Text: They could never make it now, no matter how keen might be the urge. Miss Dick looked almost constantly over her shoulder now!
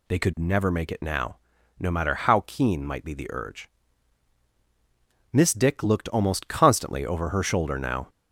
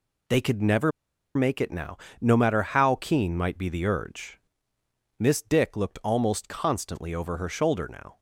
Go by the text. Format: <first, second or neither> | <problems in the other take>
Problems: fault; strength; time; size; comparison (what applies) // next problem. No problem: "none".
first | pauses between "never" and "make"; at 0.9 s; 0.44 s long